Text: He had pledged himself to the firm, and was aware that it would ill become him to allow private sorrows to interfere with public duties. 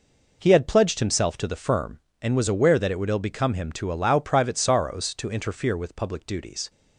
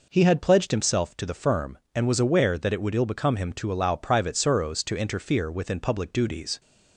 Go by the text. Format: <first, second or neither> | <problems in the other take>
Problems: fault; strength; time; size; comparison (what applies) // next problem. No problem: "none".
first | says "within" for "with"; at 5.5 s